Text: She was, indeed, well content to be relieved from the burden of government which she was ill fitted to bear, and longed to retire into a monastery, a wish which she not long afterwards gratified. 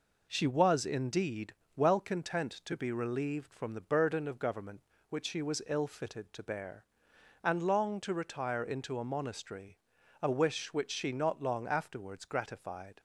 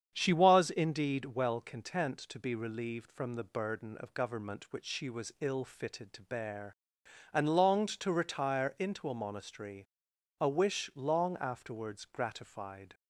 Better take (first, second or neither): first